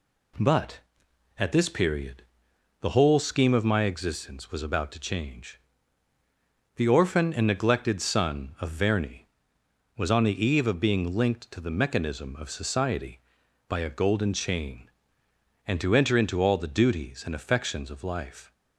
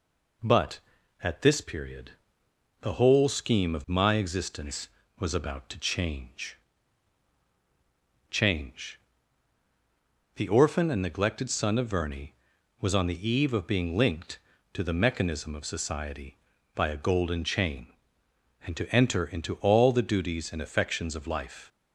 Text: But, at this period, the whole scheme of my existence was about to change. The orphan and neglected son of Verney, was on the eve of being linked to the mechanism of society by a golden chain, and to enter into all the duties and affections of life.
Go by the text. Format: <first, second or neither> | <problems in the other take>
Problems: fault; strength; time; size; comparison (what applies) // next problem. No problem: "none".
first | says "change" twice; at 8.3 s